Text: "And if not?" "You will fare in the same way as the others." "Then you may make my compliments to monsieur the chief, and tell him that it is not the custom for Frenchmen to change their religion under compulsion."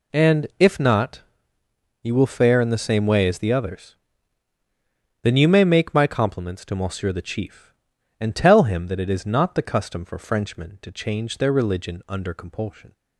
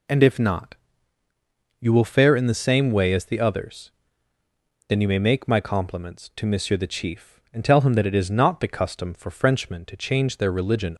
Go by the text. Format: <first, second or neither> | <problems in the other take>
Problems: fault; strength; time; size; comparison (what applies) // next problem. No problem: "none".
first | stops before "under compulsion"; at 10.9 s